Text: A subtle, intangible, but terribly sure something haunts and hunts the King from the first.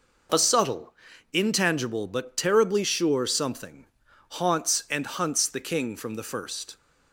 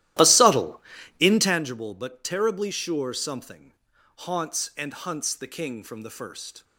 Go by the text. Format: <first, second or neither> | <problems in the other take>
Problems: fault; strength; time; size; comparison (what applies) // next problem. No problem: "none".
first | starts louder than the rest; strong; until 1.7 s; 14.5 dB // pauses between "something" and "haunts"; at 3.7 s; 0.42 s long; also in the first